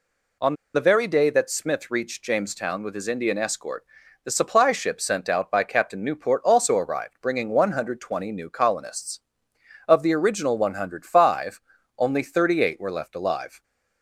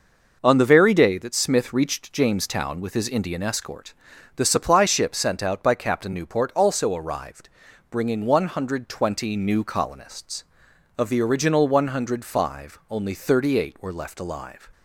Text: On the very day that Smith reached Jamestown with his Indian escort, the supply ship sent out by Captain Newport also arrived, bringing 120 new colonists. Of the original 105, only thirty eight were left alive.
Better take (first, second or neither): second